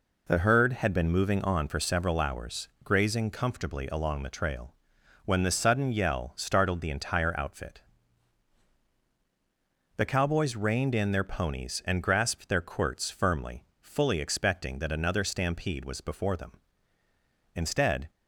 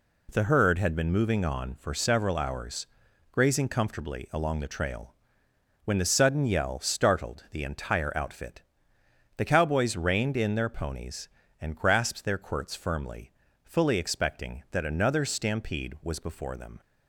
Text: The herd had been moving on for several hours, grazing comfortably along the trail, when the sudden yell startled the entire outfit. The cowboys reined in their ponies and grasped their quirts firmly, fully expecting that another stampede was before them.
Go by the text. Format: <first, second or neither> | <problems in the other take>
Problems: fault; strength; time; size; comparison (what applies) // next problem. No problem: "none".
second | goes on to say "Instead"; from 17.5 s on; 0.54 s long